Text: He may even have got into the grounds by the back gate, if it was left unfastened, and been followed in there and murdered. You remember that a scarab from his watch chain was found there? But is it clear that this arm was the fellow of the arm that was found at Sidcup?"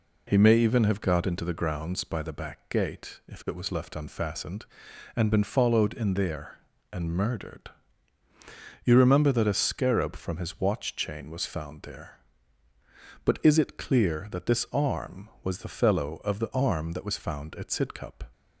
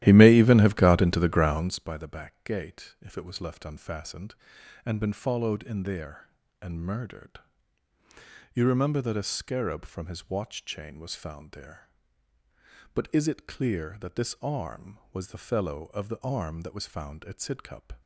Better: first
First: none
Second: starts louder than the rest; strong; until 1.8 s; 14 dB

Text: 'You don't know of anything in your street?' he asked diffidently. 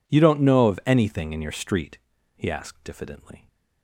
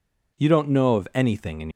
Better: first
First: none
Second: stops before "your street he asked diffidently"; at 1.6 s

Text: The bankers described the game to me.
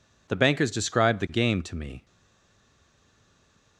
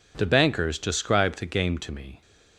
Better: second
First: stays silent after the last word; noticeable; from 2.0 s on; 1.7 s long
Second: none

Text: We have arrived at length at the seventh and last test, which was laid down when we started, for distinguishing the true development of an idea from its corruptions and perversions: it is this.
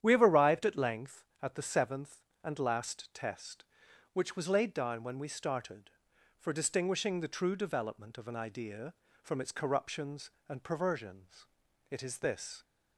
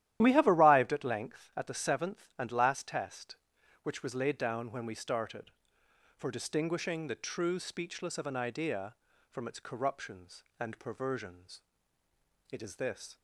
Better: first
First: starts louder than the rest; strong; until 1.0 s; 10 dB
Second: starts louder than the rest; strong; until 1.2 s; 12.5 dB // says "speechless" for "development"; at 7.5 s

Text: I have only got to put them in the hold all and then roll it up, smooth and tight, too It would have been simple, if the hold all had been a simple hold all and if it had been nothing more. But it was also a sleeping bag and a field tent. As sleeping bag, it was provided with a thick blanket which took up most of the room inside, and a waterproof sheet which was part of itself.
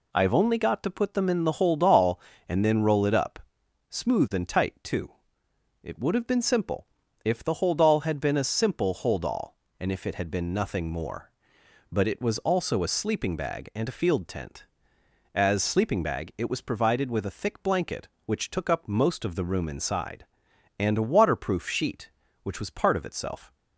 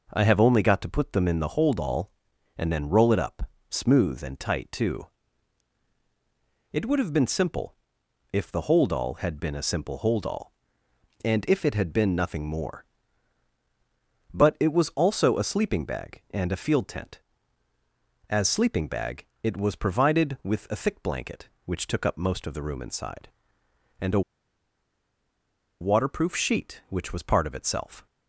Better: first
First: pauses between "too" and "It"; noticeable; at 5.1 s; 0.70 s long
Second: pauses between "too" and "It"; strong; at 5.0 s; 1.6 s long // pauses between "a" and "waterproof"; strong; at 24.2 s; 1.6 s long

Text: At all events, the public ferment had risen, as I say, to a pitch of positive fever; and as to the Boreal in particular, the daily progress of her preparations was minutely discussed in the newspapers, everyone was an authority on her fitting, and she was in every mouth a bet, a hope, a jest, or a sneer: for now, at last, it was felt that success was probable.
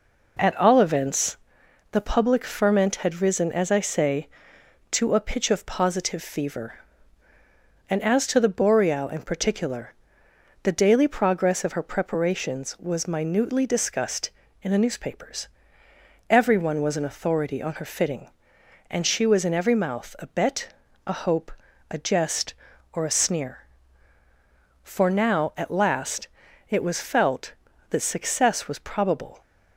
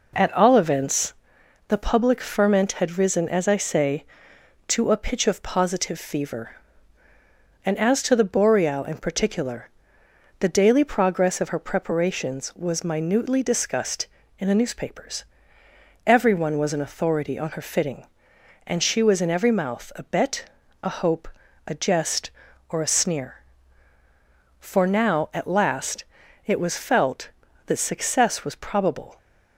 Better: neither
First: none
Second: none

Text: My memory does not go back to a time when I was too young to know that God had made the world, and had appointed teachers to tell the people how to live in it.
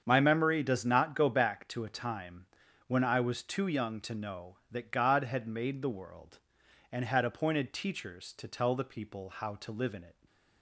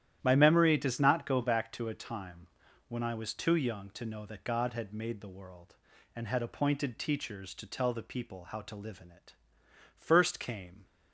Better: first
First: starts louder than the rest; strong; until 1.0 s; 7.5 dB // pauses between "time" and "when"; at 2.4 s; 0.42 s long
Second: starts louder than the rest; strong; until 1.2 s; 11.5 dB // pauses between "time" and "when"; at 2.4 s; 0.42 s long // goes on to say "First came"; noticeable; from 9.9 s on; 0.88 s long

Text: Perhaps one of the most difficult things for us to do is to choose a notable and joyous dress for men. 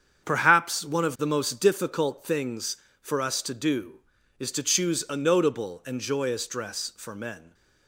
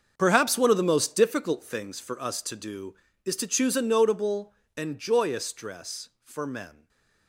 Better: first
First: starts louder than the rest; strong; until 1.2 s; 7.5 dB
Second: gets quieter; strong; throughout; 14.5 dB // starts louder than the rest; until 1.1 s; 6 dB // stays silent after the last word; slight; from 6.7 s on; 0.5 s long

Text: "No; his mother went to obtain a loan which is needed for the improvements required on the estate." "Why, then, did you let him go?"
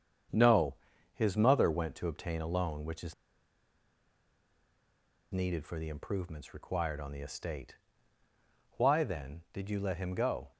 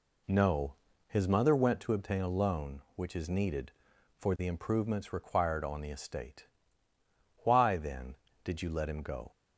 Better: second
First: starts louder than the rest; strong; until 1.7 s; 7.5 dB // pauses between "is" and "needed"; strong; at 3.1 s; 2.1 s long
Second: none

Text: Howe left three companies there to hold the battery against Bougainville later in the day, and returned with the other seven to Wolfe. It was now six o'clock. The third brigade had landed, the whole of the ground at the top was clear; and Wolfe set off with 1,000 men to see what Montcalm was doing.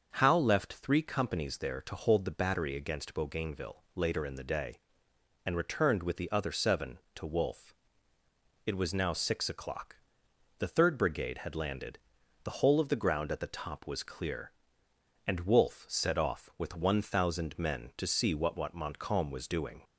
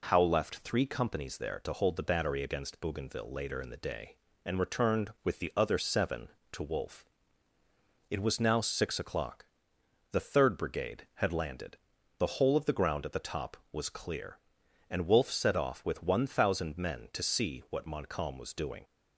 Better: second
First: starts louder than the rest; until 1.1 s; 6.5 dB // says "what" twice; at 18.5 s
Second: none

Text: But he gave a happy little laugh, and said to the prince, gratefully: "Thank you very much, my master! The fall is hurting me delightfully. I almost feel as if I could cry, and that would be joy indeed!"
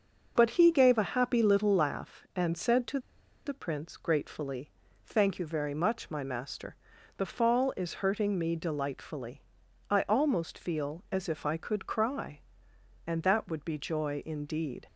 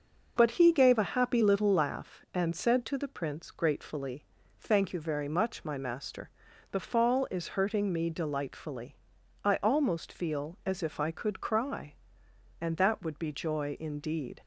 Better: second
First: pauses between "to" and "the"; noticeable; at 2.9 s; 0.47 s long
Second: none

